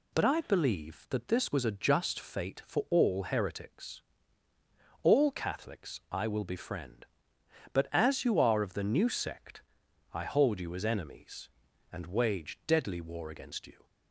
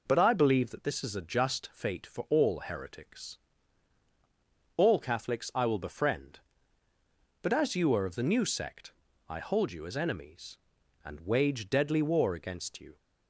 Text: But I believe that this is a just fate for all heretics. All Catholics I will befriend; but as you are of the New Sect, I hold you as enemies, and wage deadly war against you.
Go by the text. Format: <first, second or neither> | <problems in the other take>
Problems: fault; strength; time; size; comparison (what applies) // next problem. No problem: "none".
second | says "was" for "is"; at 1.5 s